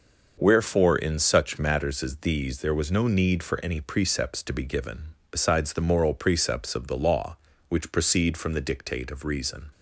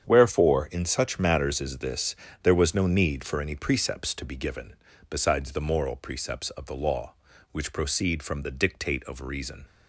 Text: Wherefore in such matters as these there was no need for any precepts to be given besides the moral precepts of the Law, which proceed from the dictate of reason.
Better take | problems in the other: first | starts louder than the rest; strong; until 1.0 s; 8 dB; also in the first // says "this" for "these"; at 1.7 s // pauses between "given" and "besides"; slight; at 4.7 s; 0.34 s long; slight in the first

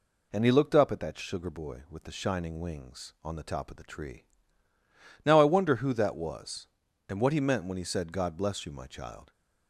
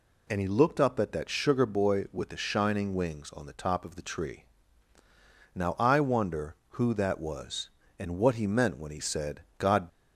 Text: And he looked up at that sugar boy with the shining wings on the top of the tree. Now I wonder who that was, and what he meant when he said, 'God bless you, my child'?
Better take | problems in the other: first | stops before "bless you my child"; at 9.8 s

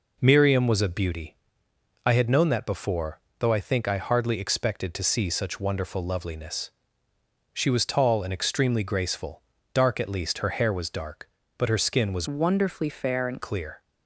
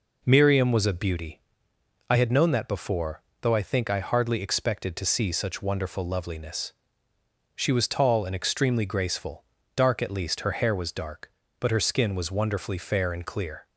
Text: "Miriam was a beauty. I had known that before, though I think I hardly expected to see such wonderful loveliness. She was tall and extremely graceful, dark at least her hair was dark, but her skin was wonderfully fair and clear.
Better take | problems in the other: second | changes voice from "wonderfully" to "and"; from 12.2 to 13.4 s; 1.2 s long

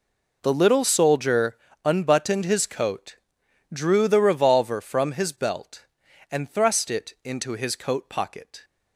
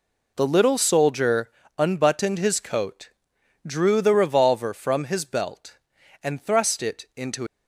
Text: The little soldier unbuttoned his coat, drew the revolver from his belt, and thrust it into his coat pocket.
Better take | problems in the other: first | pauses between "soldier" and "unbuttoned"; slight; at 1.5 s; 0.26 s long; slight in the first // stops before "his coat pocket"; at 7.4 s

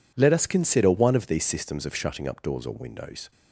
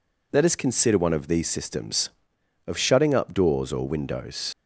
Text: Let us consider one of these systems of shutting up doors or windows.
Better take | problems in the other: first | leaves "windows" unfinished; at 4.5 s; 50 ms

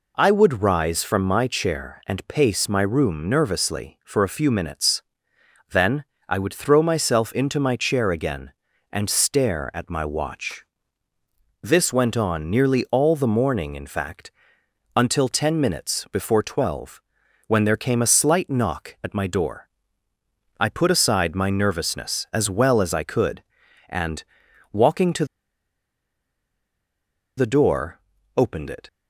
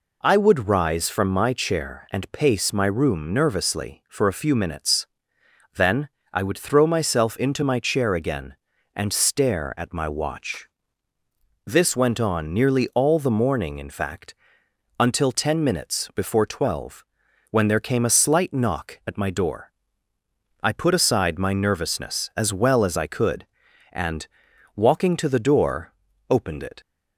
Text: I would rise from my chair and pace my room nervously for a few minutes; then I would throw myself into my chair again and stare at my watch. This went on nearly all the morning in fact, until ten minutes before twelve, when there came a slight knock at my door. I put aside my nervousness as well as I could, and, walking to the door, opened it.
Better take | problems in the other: second | pauses between "then" and "I"; slight; at 6.0 s; 0.24 s long; slight in the second // pauses between "minutes" and "before"; slight; at 15.9 s; 0.20 s long; slight in the second // pauses between "to" and "the"; strong; at 25.2 s; 2.1 s long

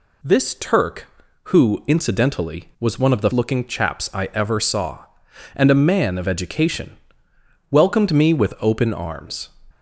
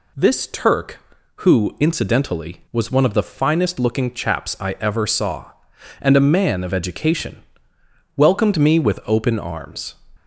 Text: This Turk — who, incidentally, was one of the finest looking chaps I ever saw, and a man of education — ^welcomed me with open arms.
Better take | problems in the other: second | skips "finest"; at 3.3 s

